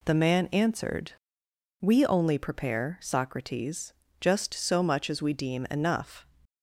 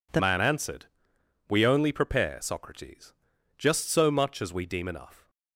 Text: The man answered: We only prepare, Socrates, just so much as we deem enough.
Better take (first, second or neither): first